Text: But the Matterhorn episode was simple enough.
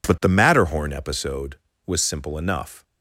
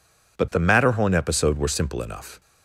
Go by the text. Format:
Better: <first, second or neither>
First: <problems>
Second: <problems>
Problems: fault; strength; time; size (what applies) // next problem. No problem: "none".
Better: first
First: none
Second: says "were" for "was"; at 1.5 s